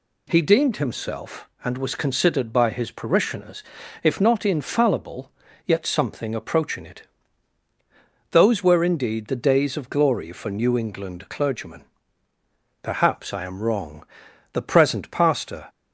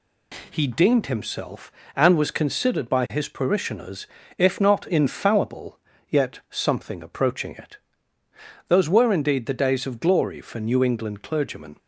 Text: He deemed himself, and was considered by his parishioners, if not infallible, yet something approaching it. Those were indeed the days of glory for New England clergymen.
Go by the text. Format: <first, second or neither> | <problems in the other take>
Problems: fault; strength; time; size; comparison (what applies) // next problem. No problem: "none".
second | goes on to say "Perhaps I am wrong The present pastor"; strong; from 12.8 s on; 2.8 s long